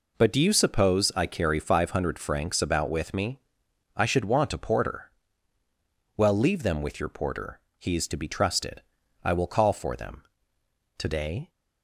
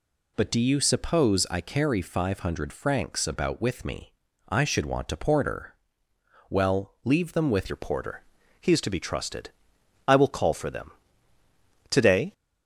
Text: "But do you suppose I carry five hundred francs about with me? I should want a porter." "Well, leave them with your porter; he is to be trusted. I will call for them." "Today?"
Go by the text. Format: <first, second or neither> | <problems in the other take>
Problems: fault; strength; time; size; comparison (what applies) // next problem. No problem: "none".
first | changes voice at "your"; from 7.6 s on; 4.7 s long